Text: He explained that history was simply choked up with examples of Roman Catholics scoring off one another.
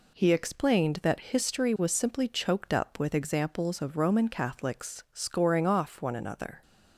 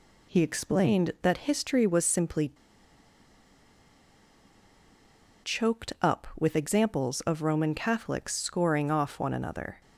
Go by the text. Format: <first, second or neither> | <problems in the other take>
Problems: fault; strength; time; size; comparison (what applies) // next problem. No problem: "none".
first | pauses between "simply" and "choked"; strong; at 2.5 s; 2.9 s long